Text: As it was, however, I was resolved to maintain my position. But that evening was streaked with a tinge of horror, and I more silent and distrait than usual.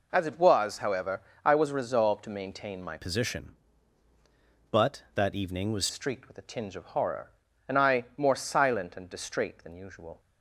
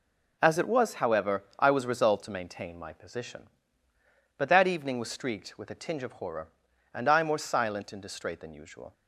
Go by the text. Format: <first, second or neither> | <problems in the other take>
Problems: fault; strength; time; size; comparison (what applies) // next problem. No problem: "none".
second | changes voice from "position" to "was"; from 2.9 to 5.8 s; 2.9 s long